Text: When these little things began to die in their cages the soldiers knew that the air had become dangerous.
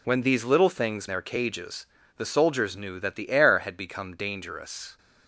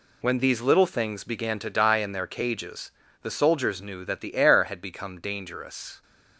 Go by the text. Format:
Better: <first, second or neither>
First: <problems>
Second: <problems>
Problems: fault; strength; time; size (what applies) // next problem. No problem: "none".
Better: second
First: skips "began to die in"; at 1.0 s // pauses between "cages" and "the"; slight; at 1.8 s; 0.30 s long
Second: pauses between "cages" and "the"; slight; at 2.9 s; 0.30 s long